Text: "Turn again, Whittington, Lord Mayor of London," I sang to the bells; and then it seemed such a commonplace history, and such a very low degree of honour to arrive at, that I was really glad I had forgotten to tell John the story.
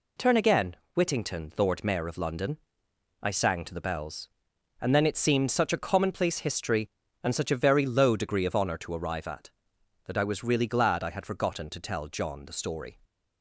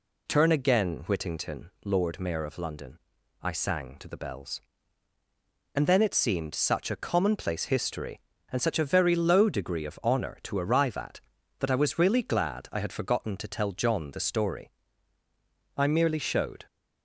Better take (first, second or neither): first